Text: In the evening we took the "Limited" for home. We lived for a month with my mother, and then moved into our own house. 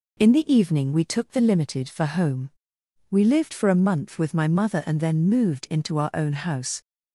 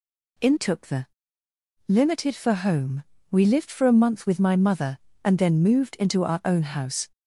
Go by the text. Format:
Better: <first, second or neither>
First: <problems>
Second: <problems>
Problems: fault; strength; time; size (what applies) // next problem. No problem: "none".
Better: first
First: none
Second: skips "the evening we"; at 0.5 s // pauses between "the" and "Limited"; noticeable; at 1.0 s; 0.82 s long